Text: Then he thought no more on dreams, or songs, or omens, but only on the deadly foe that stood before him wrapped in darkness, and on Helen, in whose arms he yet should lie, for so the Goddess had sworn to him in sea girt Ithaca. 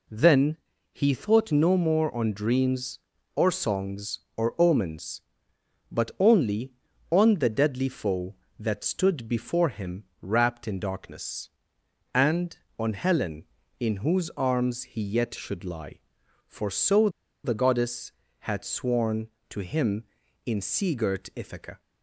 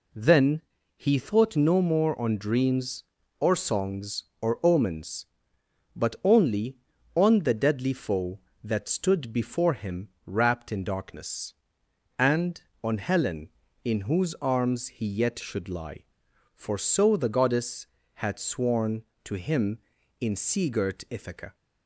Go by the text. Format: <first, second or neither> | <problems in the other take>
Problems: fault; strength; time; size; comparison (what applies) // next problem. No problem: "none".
second | pauses between "Then" and "he"; slight; at 0.5 s; 0.34 s long; slight in the second // pauses between "him" and "wrapped"; slight; at 10.0 s; 0.18 s long; slight in the second // pauses between "so" and "the"; slight; at 17.0 s; 0.35 s long